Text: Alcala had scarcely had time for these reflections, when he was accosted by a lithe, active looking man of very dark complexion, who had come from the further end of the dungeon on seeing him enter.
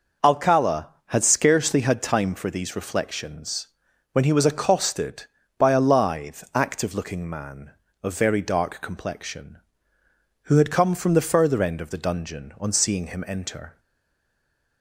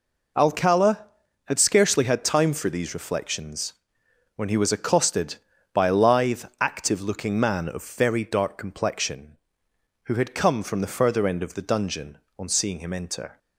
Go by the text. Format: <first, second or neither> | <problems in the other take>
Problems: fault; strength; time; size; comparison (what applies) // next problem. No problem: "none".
second | stays silent after the last word; from 13.7 s on; 1.1 s long